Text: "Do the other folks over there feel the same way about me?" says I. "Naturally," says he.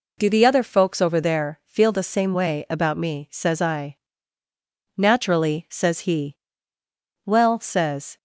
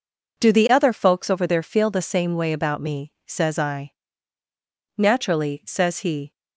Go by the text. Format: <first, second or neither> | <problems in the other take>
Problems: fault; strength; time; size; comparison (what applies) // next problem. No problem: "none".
second | goes on to say "Well says"; noticeable; from 7.2 s on; 0.90 s long